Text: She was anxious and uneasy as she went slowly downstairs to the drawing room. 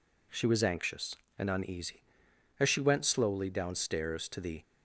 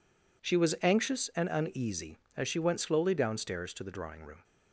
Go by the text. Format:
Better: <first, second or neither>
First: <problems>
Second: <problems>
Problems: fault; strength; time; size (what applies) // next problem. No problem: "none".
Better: second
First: stops before "drawing room"; at 4.6 s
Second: none